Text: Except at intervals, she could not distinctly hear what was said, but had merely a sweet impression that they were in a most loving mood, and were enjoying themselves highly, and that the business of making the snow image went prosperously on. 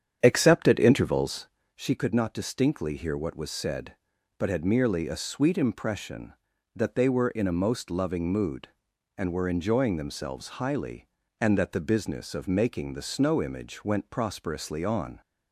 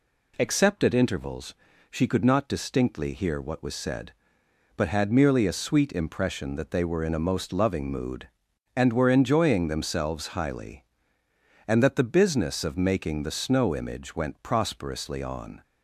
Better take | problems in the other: second | starts louder than the rest; strong; until 1.6 s; 8.5 dB

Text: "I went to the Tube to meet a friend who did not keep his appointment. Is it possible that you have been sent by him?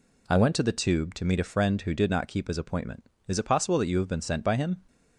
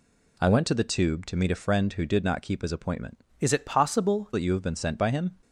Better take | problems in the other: first | changes voice from "Is" to "possible"; from 3.4 to 4.2 s; 0.8 s long

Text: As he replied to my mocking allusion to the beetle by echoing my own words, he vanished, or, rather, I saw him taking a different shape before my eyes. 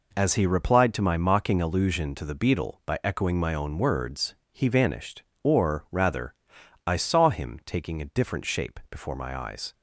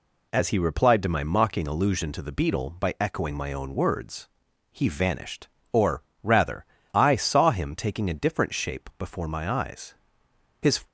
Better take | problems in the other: first | goes on to say "His"; slight; from 10.6 s on; 0.26 s long

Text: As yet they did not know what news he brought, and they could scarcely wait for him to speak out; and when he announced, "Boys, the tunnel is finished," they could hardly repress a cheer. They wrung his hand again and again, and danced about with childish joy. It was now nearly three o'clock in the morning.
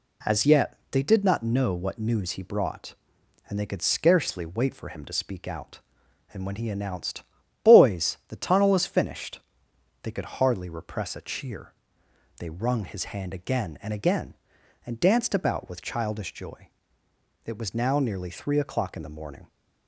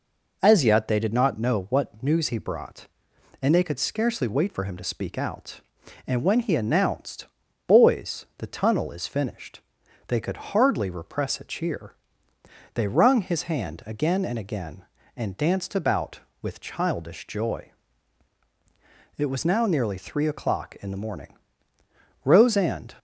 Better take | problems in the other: first | goes on to say "Rose and"; noticeable; from 22.2 s on; 0.72 s long

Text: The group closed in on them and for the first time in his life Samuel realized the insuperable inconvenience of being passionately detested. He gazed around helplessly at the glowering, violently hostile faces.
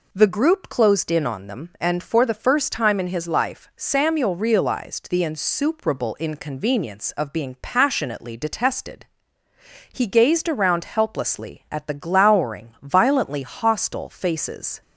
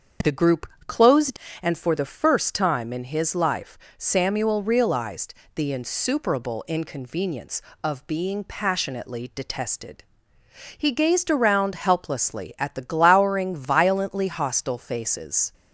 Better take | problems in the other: first | starts louder than the rest; until 1.6 s; 7 dB // pauses between "group" and "closed"; slight; at 0.6 s; 0.16 s long // skips "in on them"; at 1.4 s // pauses between "life" and "Samuel"; slight; at 3.7 s; 0.18 s long // pauses between "realized" and "the"; slight; at 5.3 s; 0.22 s long

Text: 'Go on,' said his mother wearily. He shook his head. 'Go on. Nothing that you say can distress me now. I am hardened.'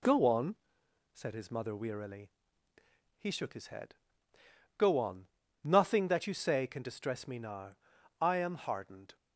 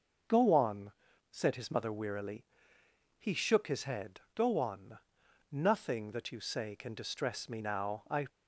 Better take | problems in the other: first | starts louder than the rest; noticeable; until 1.6 s; 6 dB // stops before "am hardened"; at 8.2 s

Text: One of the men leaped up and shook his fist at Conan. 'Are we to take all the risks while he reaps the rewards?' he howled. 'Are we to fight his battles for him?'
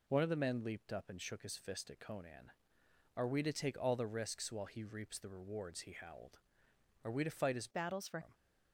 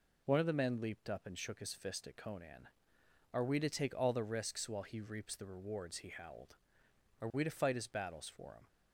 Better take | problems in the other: second | changes voice from "battles" to "for"; from 7.7 to 8.1 s; 0.4 s long

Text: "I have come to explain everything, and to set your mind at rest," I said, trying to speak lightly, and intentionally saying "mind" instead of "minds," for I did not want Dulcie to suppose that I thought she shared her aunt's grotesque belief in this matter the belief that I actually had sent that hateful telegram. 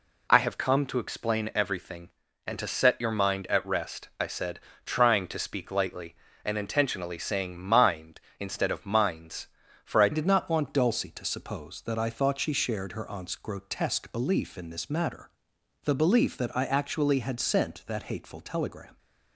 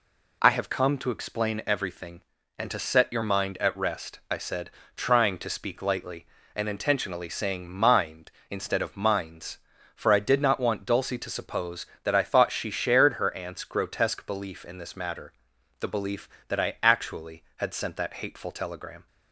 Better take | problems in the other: second | changes voice at "did"; from 10.1 s on; 8.8 s long // pauses between "matter" and "the"; noticeable; at 15.2 s; 0.54 s long; noticeable in the second

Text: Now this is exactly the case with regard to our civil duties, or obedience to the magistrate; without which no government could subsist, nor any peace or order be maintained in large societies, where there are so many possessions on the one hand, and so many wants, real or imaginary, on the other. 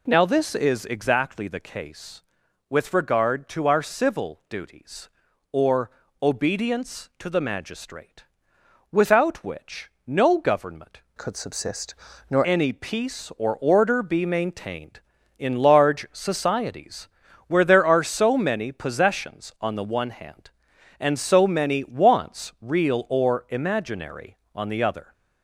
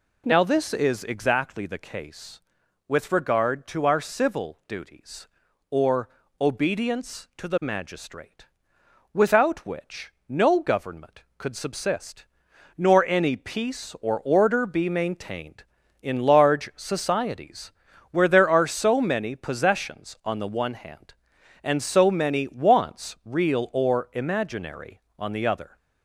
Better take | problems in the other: second | pauses between "or" and "obedience"; slight; at 5.8 s; 0.32 s long; slight in the second // pauses between "which" and "no"; slight; at 9.9 s; 0.16 s long; slight in the second // changes voice from "could" to "nor"; from 11.1 to 12.4 s; 1.3 s long

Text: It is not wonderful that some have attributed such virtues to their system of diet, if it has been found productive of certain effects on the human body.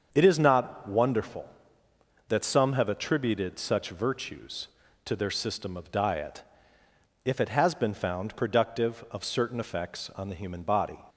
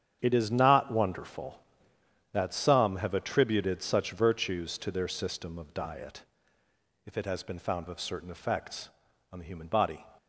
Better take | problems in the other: first | starts louder than the rest; strong; until 1.2 s; 8.5 dB; also in the first // skips "productive"; at 7.8 s

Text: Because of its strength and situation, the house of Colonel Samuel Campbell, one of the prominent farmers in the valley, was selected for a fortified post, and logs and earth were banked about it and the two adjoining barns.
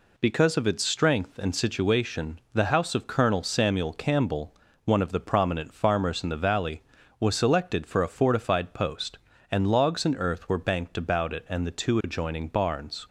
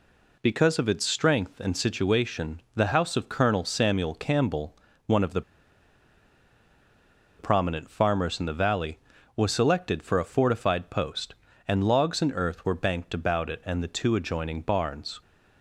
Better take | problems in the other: first | pauses between "the" and "prominent"; strong; at 5.4 s; 1.9 s long

